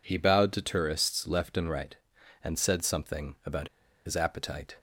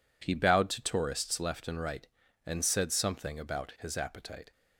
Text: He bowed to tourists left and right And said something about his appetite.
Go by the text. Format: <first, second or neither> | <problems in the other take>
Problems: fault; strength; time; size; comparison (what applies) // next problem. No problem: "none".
second | pauses between "about" and "his"; at 3.6 s; 0.37 s long